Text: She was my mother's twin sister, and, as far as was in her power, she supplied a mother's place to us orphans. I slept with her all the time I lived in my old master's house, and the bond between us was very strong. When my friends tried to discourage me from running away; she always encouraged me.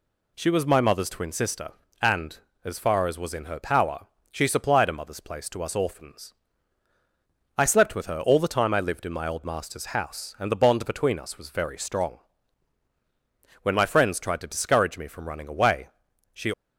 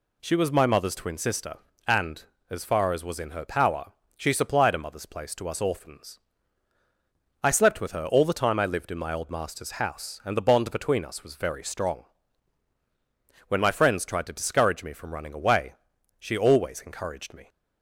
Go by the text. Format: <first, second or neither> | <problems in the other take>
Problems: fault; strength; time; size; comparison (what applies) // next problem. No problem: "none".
second | stops before "always encouraged me"; at 16.5 s